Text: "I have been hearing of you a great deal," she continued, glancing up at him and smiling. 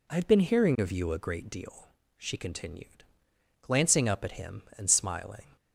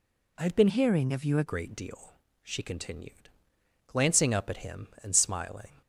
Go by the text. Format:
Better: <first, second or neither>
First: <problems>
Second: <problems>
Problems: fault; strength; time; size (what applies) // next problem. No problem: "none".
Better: first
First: none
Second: changes voice from "hearing" to "a"; from 0.6 to 1.4 s; 0.8 s long